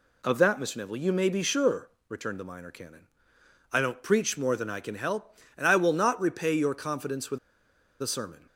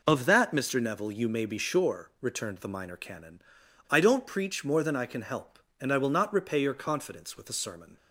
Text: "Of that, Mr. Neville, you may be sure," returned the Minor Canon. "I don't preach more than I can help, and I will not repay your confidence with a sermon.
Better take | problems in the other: second | pauses between "with" and "a"; noticeable; at 7.3 s; 0.63 s long

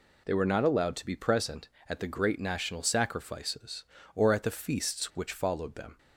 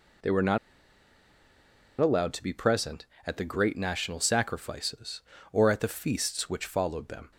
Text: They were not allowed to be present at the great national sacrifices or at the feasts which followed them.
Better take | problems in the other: first | pauses between "not" and "allowed"; strong; at 0.5 s; 1.4 s long

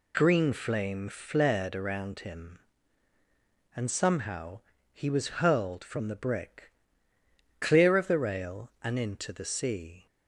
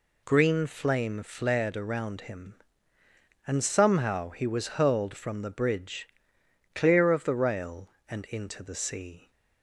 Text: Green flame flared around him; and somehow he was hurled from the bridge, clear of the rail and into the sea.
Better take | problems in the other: second | pauses between "somehow" and "he"; slight; at 4.5 s; 0.34 s long // says "brick" for "bridge"; at 6.1 s

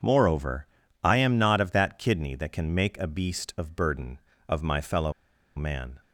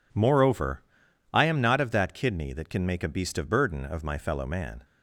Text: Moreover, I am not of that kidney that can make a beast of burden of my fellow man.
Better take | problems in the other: second | pauses between "fellow" and "man"; at 5.1 s; 0.44 s long

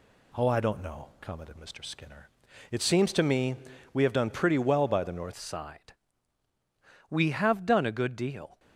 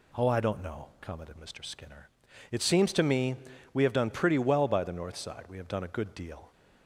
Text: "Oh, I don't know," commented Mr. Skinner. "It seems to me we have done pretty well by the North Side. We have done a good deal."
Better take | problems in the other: second | pauses between "me" and "we"; at 3.5 s; 0.38 s long; also in the second // changes voice at "Side"; from 5.3 s on; 3.2 s long

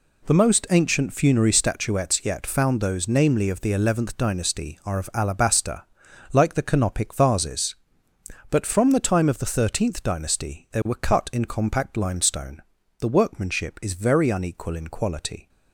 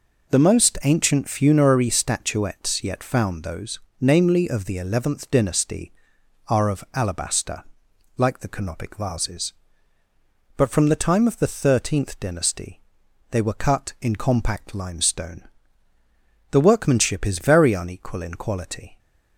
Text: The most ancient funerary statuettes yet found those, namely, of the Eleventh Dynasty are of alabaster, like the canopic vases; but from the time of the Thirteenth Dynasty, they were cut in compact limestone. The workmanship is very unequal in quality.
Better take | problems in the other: neither | none

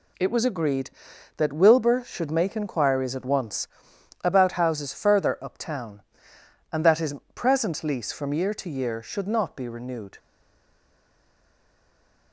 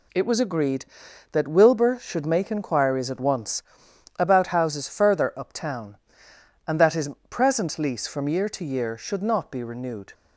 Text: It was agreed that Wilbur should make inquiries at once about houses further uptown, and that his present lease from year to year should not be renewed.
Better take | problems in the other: second | pauses between "once" and "about"; noticeable; at 3.6 s; 0.56 s long; noticeable in the second // pauses between "his" and "present"; slight; at 7.1 s; 0.18 s long; slight in the second // stays silent after the last word; from 10.1 s on; 2.2 s long

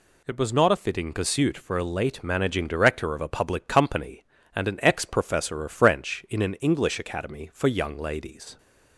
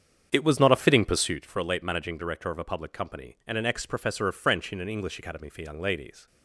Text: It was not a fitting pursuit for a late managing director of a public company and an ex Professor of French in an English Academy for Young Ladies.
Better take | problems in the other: first | starts louder than the rest; strong; until 1.5 s; 8 dB

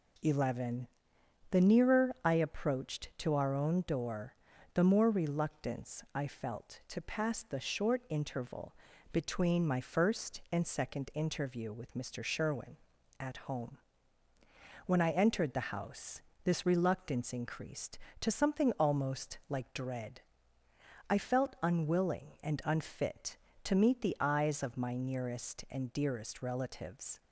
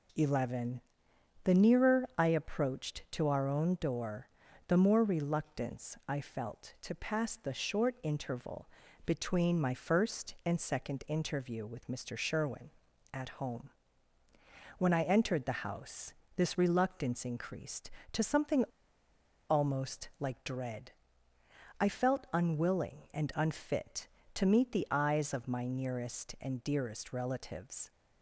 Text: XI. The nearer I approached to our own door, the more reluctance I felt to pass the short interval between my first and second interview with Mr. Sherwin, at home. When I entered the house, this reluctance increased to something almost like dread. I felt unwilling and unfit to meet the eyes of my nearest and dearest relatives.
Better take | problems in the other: first | pauses between "interval" and "between"; at 8.6 s; 0.38 s long; also in the first // pauses between "something" and "almost"; noticeable; at 18.6 s; 0.84 s long

